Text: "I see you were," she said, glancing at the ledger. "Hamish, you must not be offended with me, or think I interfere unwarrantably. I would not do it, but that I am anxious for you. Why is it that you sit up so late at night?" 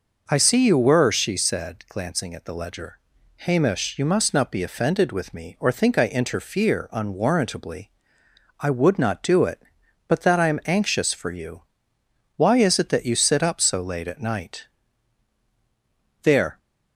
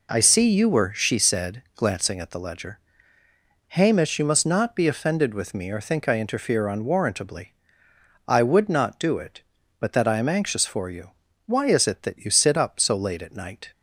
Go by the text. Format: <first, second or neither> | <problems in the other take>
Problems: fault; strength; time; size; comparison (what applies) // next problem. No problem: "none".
second | goes on to say "There"; slight; from 16.2 s on; 0.36 s long